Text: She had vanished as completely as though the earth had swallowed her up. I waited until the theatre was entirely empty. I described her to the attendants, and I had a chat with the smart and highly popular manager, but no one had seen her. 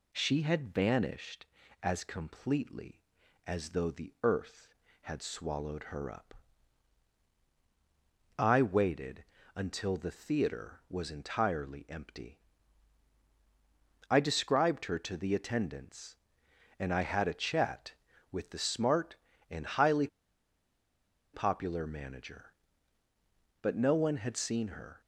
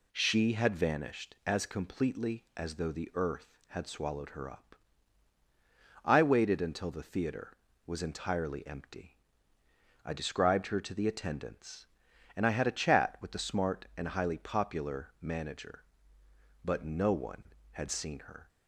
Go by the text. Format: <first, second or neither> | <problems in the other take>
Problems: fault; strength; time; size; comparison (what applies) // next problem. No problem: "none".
second | pauses between "waited" and "until"; slight; at 9.2 s; 0.30 s long // pauses between "highly" and "popular"; strong; at 20.0 s; 1.2 s long